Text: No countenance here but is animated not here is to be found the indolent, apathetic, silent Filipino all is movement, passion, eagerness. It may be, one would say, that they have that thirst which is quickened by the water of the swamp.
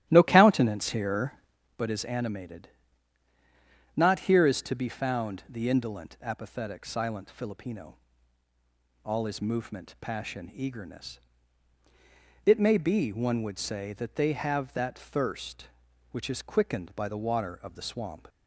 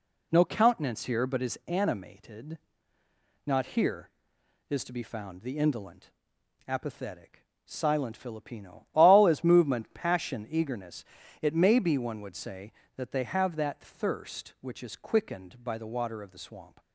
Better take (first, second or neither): second